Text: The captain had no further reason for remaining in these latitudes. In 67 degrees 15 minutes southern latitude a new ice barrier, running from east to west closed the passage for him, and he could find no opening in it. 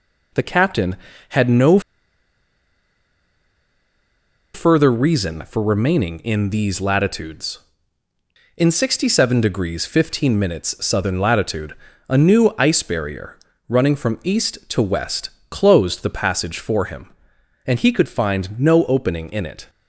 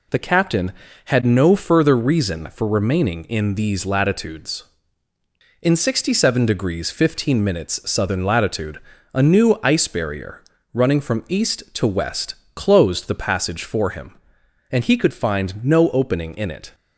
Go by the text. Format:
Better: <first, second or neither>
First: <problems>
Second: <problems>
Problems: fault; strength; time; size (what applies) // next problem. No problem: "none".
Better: second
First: pauses between "no" and "further"; strong; at 1.7 s; 2.7 s long // pauses between "latitude" and "a"; slight; at 11.7 s; 0.32 s long // pauses between "west" and "closed"; slight; at 15.2 s; 0.20 s long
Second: pauses between "latitude" and "a"; slight; at 8.8 s; 0.32 s long // pauses between "west" and "closed"; slight; at 12.3 s; 0.20 s long